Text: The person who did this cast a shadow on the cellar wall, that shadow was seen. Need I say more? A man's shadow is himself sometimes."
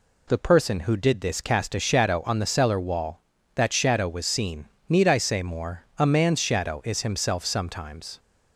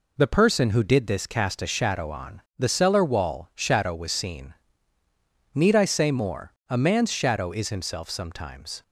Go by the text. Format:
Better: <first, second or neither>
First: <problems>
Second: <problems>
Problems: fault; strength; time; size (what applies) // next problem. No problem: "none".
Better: first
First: none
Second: pauses between "on" and "the"; slight; at 2.4 s; 0.18 s long // skips "that"; at 3.5 s